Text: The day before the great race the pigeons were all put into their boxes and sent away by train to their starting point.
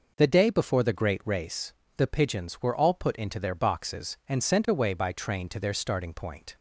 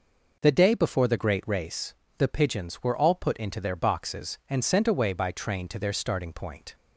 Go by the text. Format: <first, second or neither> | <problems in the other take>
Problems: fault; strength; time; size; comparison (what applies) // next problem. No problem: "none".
neither | pauses between "race" and "the"; slight; the same in both